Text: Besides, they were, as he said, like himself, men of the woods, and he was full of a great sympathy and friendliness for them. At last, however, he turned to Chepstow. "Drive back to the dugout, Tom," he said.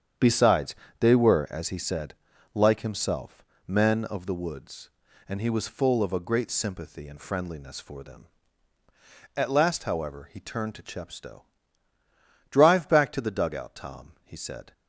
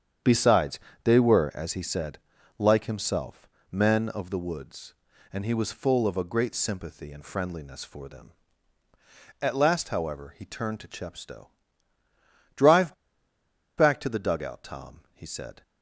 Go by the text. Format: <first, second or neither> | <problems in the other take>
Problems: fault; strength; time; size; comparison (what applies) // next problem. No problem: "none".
first | starts louder than the rest; strong; until 1.4 s; 8 dB; strong in the first // pauses between "Drive" and "back"; noticeable; at 12.9 s; 0.84 s long